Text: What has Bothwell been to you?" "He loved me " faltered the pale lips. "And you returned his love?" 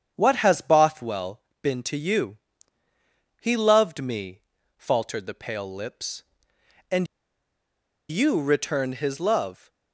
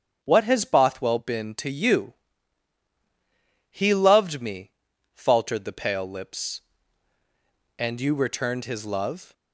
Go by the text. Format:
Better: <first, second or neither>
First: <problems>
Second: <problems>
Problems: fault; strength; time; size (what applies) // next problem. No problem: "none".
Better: second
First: starts louder than the rest; strong; until 1.1 s; 8 dB // pauses between "Bothwell" and "been"; slight; at 1.4 s; 0.20 s long // pauses between "And" and "you"; at 7.0 s; 1.0 s long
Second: starts louder than the rest; until 1.2 s; 7 dB